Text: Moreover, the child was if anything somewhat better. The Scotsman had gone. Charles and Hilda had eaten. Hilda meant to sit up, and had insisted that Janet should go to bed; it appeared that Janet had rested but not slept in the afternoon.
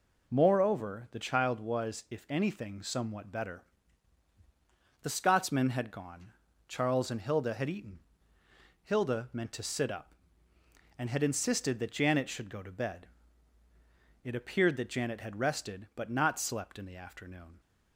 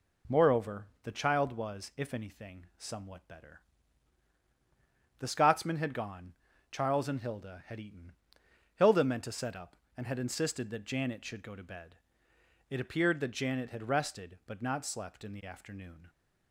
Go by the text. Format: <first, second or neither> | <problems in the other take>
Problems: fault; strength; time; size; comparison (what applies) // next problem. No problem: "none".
first | says "set" for "sit"; at 9.3 s